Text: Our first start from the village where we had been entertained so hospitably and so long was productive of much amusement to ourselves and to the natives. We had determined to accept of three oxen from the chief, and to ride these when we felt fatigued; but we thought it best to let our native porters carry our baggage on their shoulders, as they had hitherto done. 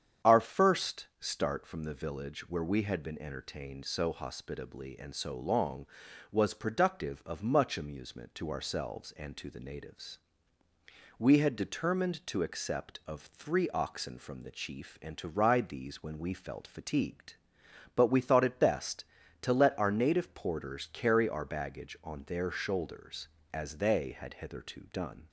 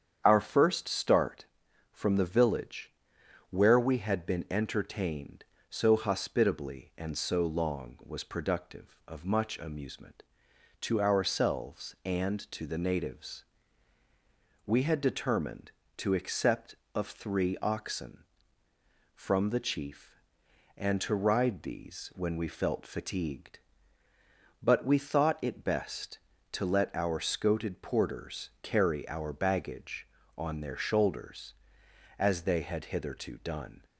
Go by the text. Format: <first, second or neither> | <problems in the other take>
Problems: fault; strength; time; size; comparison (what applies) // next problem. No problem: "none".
first | starts louder than the rest; strong; until 1.2 s; 8.5 dB; strong in the first // pauses between "village" and "where"; noticeable; at 2.9 s; 0.58 s long // says "scoted" for "native"; at 27.1 s